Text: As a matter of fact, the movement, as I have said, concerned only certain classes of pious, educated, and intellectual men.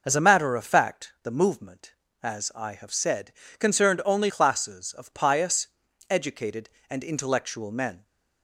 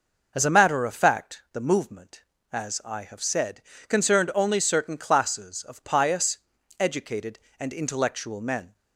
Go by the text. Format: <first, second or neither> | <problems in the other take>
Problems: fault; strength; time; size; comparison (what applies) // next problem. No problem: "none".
second | skips "certain"; at 4.2 s